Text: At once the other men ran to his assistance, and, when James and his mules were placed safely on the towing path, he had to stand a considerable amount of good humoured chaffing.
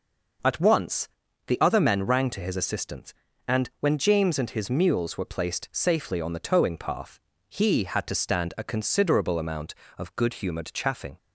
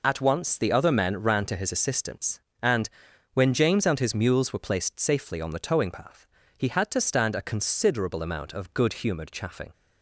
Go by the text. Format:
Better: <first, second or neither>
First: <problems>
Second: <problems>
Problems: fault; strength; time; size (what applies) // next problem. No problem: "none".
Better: second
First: pauses between "once" and "the"; at 1.0 s; 0.40 s long // says "rang" for "ran"; at 2.0 s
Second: none